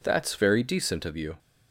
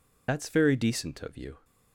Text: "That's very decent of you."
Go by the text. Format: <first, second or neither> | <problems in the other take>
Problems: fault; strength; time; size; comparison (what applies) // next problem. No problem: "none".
first | loses the start of "That's"; at 0.2 s; 130 ms